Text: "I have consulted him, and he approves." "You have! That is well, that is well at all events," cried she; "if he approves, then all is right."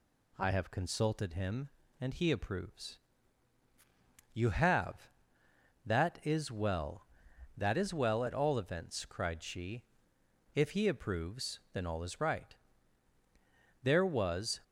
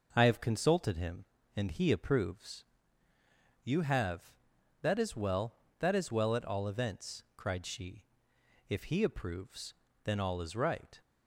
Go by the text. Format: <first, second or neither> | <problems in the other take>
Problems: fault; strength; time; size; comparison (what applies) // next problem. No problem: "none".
second | goes on to say "There was"; noticeable; from 13.8 s on; 0.80 s long